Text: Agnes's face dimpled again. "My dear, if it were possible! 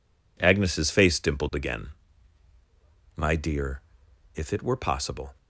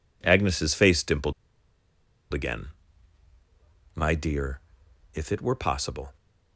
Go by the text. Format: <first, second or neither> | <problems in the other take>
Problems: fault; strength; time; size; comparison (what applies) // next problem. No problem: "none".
first | pauses between "dimpled" and "again"; at 1.3 s; 0.99 s long